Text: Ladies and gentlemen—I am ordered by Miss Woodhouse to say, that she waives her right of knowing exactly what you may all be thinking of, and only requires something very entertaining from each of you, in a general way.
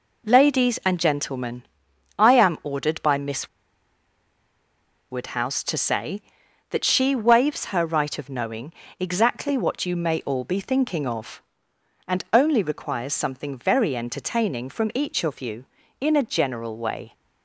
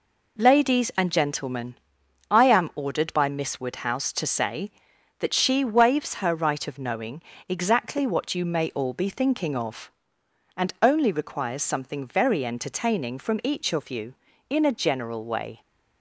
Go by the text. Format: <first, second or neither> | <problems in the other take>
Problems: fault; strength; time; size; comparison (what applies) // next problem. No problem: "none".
second | pauses between "Miss" and "Woodhouse"; strong; at 3.4 s; 1.6 s long // pauses between "knowing" and "exactly"; slight; at 8.7 s; 0.26 s long; slight in the second